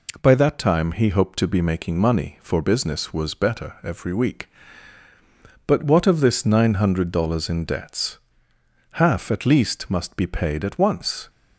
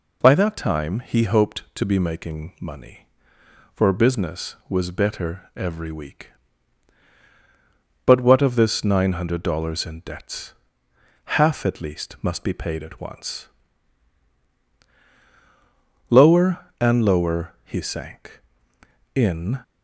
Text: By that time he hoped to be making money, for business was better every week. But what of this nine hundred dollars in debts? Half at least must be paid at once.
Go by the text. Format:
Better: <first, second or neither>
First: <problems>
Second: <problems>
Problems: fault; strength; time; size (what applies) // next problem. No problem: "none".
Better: first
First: none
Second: goes on to say "Lower and lower he sank in"; strong; from 16.1 s on; 3.5 s long